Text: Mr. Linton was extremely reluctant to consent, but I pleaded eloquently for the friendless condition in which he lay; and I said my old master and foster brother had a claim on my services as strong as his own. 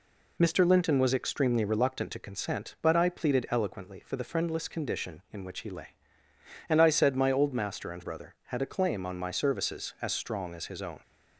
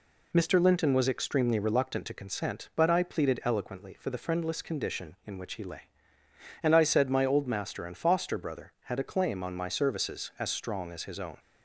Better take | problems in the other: second | skips "foster"; at 8.0 s

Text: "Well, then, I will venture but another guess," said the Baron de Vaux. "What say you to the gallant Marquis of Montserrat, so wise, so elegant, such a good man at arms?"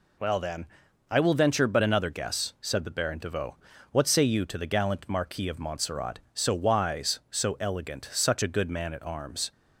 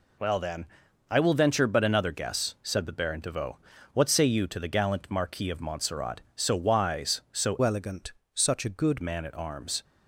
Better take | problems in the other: first | changes voice from "elegant" to "good"; from 7.6 to 9.0 s; 1.4 s long

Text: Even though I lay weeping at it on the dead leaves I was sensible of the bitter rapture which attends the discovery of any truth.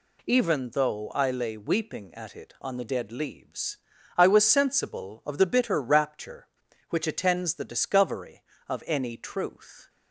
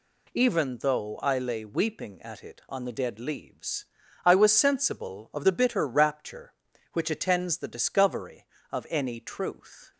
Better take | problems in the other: neither | pauses between "leaves" and "I"; the same in both

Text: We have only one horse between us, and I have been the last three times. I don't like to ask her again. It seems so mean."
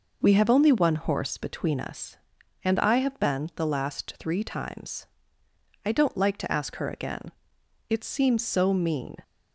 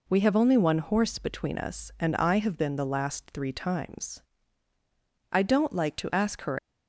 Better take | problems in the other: first | stops before "again It seems so mean"; at 6.5 s

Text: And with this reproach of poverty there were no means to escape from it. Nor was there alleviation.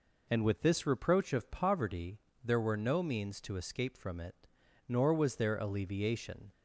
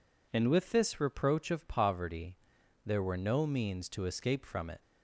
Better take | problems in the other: first | pauses between "poverty" and "there"; noticeable; at 2.3 s; 0.50 s long; slight in the first // stops before "Nor was there alleviation"; at 4.8 s

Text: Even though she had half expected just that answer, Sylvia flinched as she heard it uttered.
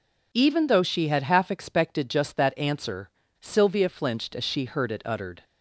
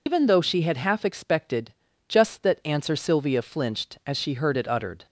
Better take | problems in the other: first | loses the start of "Even"; at 0.0 s; 100 ms // pauses between "expected" and "just"; slight; at 1.7 s; 0.36 s long

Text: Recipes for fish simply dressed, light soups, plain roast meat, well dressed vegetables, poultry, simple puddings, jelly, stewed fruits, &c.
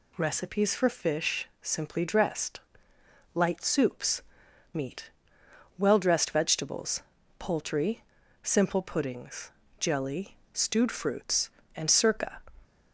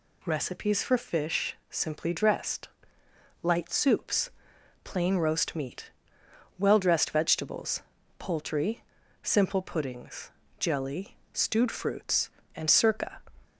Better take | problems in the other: second | pauses between "fish" and "simply"; slight; at 1.4 s; 0.16 s long; slight in the second // skips "plain roast"; at 4.4 s

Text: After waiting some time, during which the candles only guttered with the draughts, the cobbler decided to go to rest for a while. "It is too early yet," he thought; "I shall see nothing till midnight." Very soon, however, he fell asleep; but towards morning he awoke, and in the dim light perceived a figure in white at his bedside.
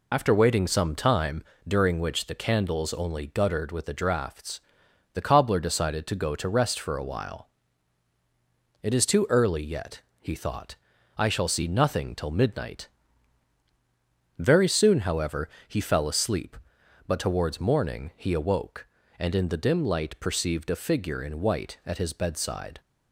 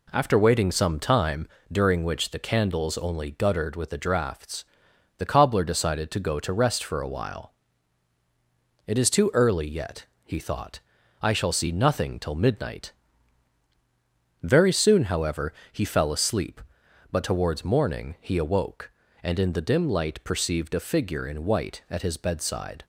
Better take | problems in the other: second | loses the start of "After"; at 0.1 s; 85 ms

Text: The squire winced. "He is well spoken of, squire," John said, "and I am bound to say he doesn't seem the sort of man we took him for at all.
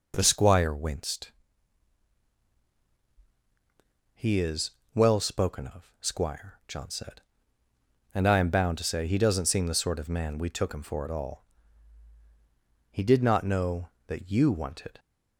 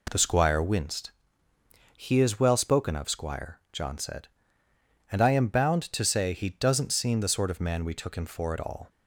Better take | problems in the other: second | pauses between "is" and "well"; slight; at 4.7 s; 0.24 s long // goes on to say "He did not know that you wanted"; strong; from 12.9 s on; 2.0 s long

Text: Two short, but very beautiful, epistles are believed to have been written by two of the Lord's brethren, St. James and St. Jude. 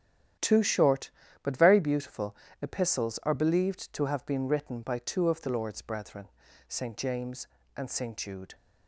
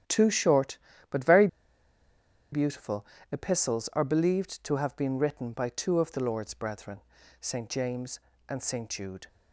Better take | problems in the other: first | starts louder than the rest; strong; until 1.3 s; 10 dB; strong in the first // pauses between "very" and "beautiful"; at 1.4 s; 1.0 s long

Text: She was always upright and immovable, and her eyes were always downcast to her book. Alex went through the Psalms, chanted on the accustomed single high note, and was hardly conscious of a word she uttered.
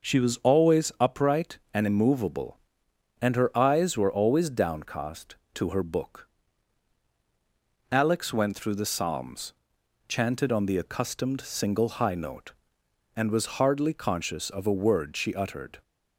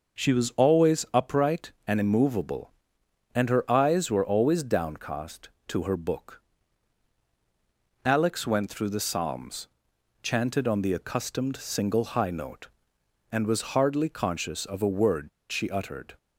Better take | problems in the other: first | pauses between "word" and "she"; slight; at 15.2 s; 0.21 s long

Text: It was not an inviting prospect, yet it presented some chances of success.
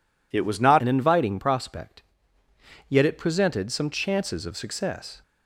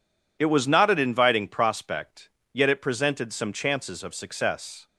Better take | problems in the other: second | changes voice at "an"; from 0.7 s on; 4.5 s long

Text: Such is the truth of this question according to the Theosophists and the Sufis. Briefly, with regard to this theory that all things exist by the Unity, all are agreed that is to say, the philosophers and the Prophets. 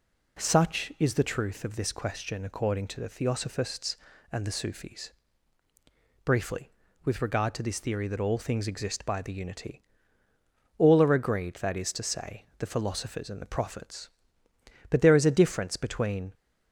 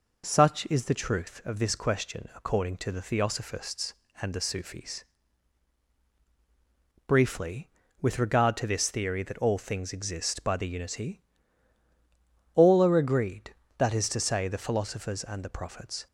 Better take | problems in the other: second | goes on to say "But there is a difference between"; from 14.9 s on; 1.4 s long

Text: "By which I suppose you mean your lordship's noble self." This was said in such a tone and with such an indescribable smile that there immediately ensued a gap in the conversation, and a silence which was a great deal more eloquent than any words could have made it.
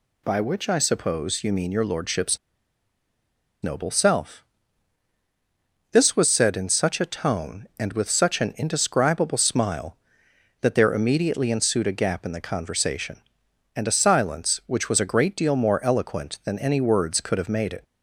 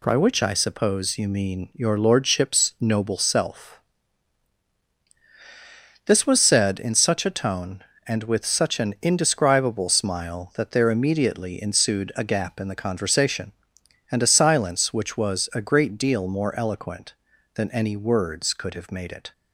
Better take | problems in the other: second | pauses between "lordship's" and "noble"; strong; at 2.3 s; 1.2 s long

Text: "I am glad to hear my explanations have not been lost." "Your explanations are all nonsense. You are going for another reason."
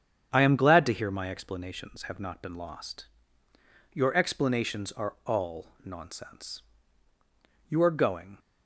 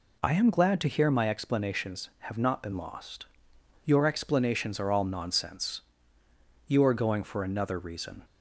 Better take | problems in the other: second | starts louder than the rest; strong; until 1.3 s; 8.5 dB // stops before "for another reason"; at 8.3 s

